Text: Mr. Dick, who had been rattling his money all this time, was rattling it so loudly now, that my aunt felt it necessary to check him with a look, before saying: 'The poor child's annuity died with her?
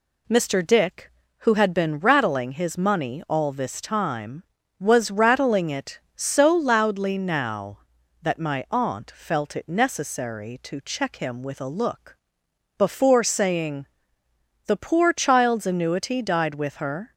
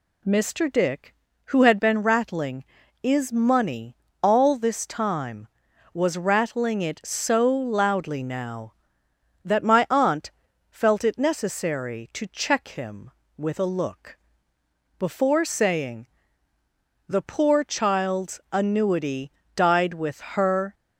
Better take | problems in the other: first | says "is" for "his"; at 3.0 s // pauses between "money" and "all"; slight; at 3.9 s; 0.26 s long // pauses between "aunt" and "felt"; at 10.2 s; 0.40 s long // pauses between "annuity" and "died"; slight; at 19.2 s; 0.24 s long

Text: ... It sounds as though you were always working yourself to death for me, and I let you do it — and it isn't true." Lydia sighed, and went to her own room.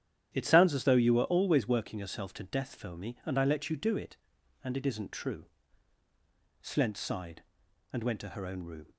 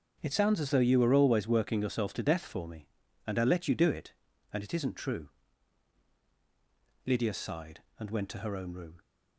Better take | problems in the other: second | starts louder than the rest; strong; until 1.3 s; 10.5 dB; also in the second // says "Slent" for "Lydia"; at 6.6 s

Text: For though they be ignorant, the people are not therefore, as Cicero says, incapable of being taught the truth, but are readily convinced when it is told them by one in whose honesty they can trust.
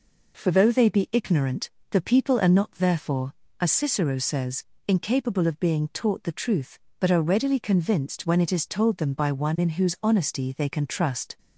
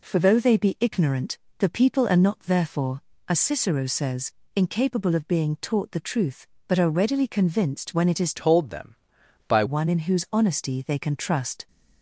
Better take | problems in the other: first | changes voice from "told" to "by"; from 8.3 to 9.6 s; 1.3 s long

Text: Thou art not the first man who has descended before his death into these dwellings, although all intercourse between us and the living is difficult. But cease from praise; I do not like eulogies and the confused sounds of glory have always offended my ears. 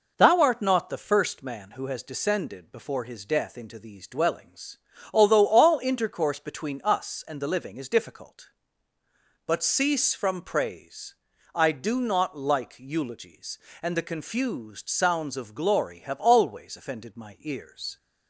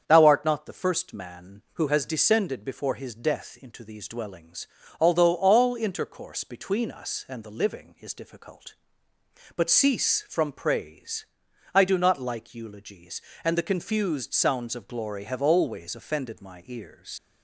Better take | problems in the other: first | starts louder than the rest; strong; until 1.0 s; 7.5 dB // leaves "ears" unfinished; at 17.1 s; 55 ms

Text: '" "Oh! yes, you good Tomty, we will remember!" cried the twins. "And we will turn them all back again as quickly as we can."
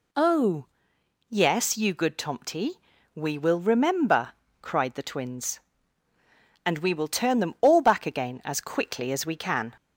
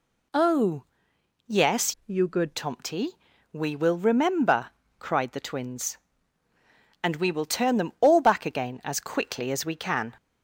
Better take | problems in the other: first | changes voice from "you" to "good"; from 2.0 to 2.5 s; 0.5 s long

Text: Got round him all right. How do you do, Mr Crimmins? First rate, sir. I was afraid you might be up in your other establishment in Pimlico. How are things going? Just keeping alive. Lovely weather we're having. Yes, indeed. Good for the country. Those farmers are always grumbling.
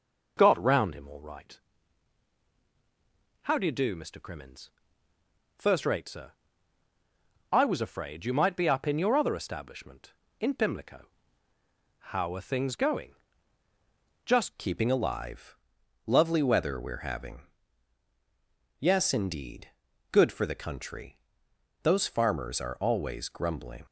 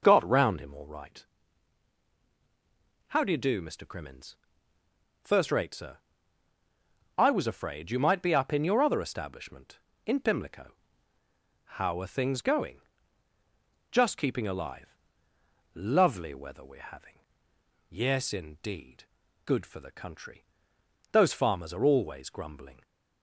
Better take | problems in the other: second | changes voice at "keeping"; from 14.5 s on; 9.3 s long

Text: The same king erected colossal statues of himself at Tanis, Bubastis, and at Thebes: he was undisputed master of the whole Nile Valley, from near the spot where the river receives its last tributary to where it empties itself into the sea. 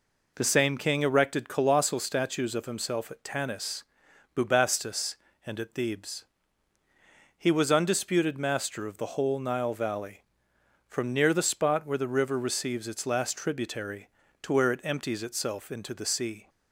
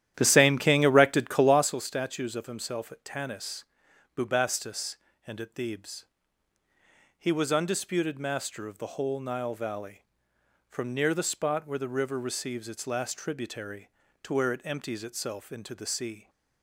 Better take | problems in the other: first | starts louder than the rest; strong; until 1.8 s; 11.5 dB

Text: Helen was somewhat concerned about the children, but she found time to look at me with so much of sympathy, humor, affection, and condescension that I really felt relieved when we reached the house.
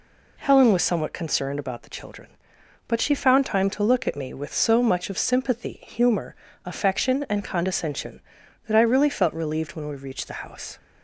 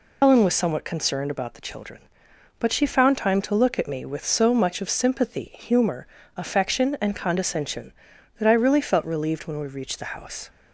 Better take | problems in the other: first | loses the start of "Helen"; at 0.2 s; 125 ms

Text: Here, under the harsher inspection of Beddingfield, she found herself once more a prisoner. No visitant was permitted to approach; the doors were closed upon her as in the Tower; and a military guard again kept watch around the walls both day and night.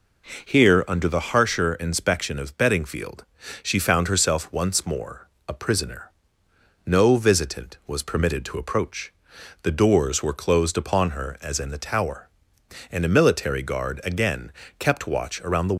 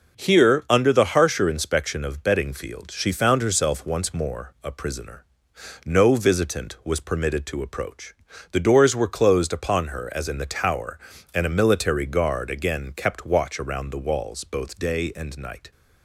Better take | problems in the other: second | pauses between "more" and "a"; slight; at 5.2 s; 0.18 s long // pauses between "again" and "kept"; slight; at 14.5 s; 0.28 s long // stops before "walls both day and night"; at 15.7 s

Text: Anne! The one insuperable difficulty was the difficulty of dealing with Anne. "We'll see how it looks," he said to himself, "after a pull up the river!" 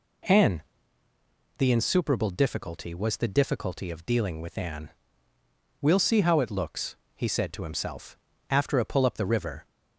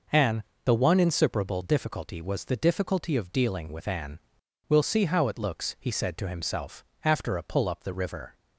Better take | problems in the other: second | skips "one"; at 1.6 s

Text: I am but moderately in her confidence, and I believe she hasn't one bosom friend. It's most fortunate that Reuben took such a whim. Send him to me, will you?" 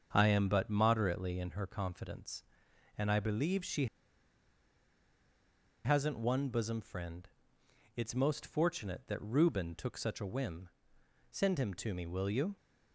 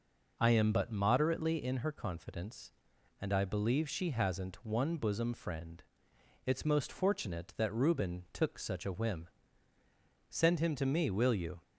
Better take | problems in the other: second | starts louder than the rest; until 1.1 s; 7 dB // pauses between "she" and "hasn't"; strong; at 3.8 s; 1.9 s long

